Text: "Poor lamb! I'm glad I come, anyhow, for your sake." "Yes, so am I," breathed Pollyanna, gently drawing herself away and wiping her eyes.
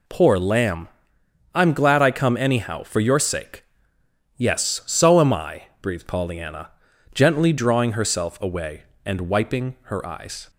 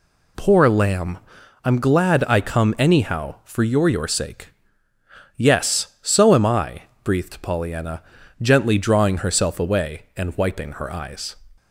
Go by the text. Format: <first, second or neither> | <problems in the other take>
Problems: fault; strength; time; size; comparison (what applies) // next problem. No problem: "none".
first | says "your" twice; at 3.8 s